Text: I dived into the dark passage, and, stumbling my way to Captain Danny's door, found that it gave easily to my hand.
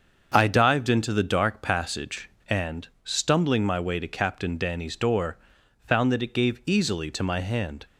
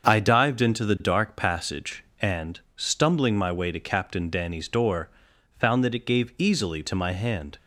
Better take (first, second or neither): neither